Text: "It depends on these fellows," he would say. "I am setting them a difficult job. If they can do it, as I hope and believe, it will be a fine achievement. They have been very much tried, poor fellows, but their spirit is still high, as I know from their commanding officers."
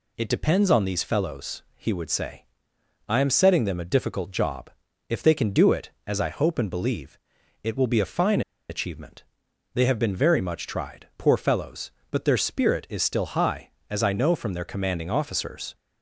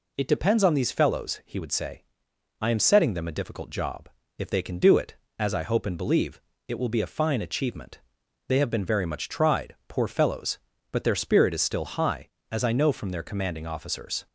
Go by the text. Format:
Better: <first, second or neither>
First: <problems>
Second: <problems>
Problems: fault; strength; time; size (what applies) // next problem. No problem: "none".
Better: second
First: pauses between "fine" and "achievement"; slight; at 8.4 s; 0.28 s long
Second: none